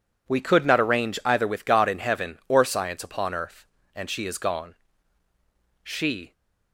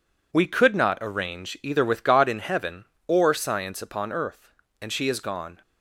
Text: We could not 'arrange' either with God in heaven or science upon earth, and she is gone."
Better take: second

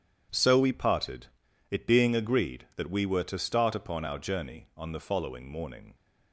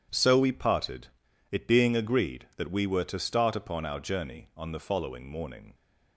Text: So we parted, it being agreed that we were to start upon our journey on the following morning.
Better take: neither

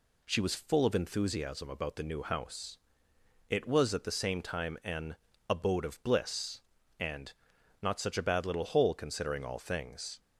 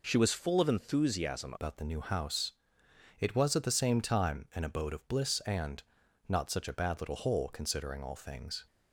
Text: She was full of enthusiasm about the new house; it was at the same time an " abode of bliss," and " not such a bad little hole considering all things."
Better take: first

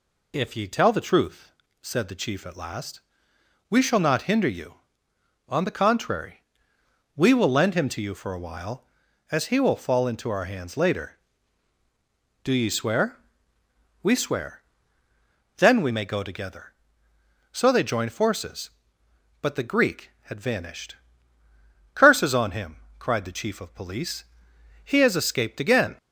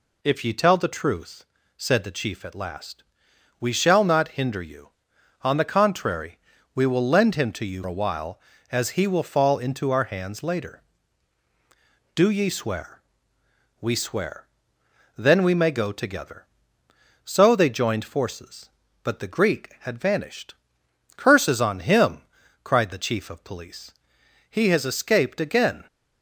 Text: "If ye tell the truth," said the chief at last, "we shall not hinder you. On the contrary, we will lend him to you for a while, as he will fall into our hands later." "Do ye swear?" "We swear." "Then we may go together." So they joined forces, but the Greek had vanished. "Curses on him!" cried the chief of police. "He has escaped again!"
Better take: first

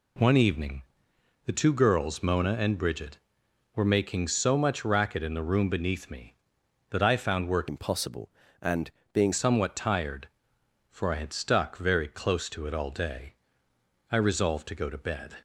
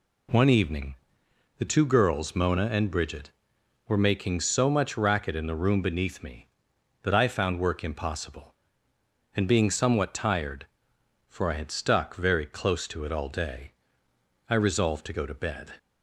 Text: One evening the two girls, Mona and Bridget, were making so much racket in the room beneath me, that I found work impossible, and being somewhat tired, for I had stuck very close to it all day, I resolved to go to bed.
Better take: second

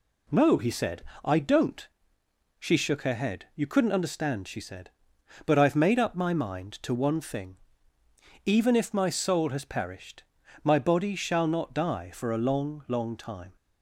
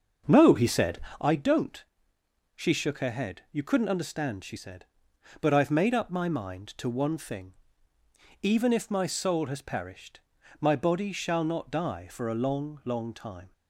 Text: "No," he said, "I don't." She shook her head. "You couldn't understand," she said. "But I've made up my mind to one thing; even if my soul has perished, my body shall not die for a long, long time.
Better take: first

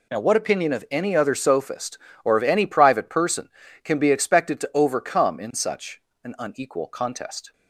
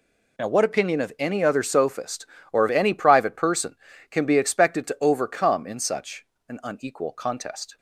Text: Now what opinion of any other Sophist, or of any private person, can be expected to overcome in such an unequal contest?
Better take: neither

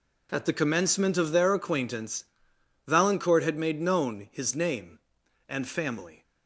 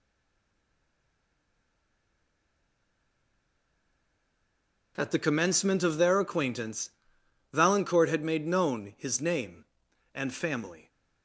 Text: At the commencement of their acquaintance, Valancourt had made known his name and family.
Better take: first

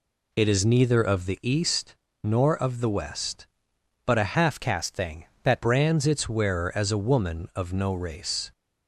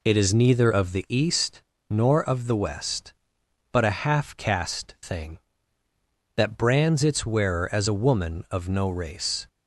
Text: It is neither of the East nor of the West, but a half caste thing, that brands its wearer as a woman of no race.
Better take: second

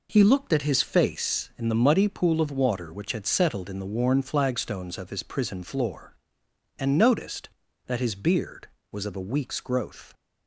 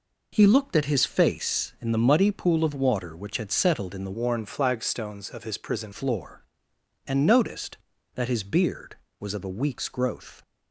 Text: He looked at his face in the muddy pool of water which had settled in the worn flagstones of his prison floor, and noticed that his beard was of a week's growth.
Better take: first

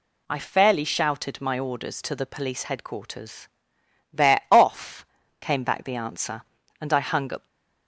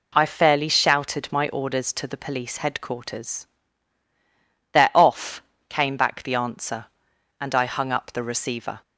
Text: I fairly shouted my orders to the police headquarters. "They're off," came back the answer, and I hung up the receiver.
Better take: second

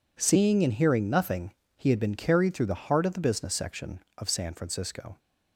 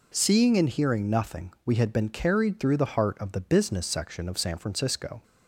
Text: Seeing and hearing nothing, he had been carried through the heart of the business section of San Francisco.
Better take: first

